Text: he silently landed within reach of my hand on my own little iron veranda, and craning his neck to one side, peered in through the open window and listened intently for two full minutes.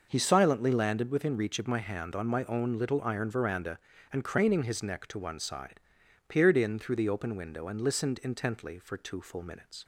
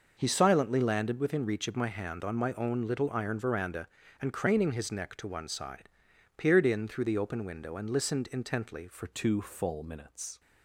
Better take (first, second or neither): first